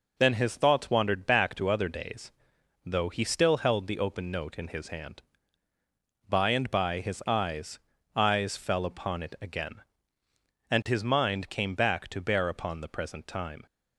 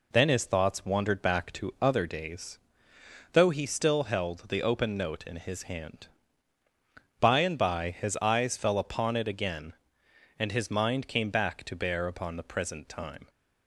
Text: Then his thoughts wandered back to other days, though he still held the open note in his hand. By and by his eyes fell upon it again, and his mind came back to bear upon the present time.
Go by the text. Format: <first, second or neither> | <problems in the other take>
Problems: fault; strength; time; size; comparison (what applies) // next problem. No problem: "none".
second | says "eyes" twice; at 8.1 s